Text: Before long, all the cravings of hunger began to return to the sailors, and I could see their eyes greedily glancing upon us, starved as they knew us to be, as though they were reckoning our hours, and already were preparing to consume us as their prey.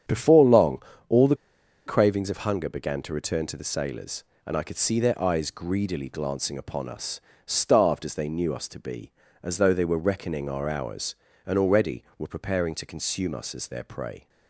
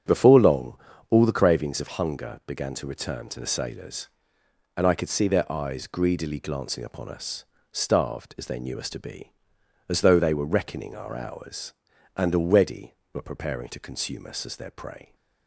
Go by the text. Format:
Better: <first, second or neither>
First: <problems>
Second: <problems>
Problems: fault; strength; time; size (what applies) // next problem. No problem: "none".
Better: second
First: starts louder than the rest; strong; until 1.3 s; 8.5 dB // pauses between "the" and "cravings"; noticeable; at 1.3 s; 0.50 s long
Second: starts louder than the rest; strong; until 1.4 s; 7.5 dB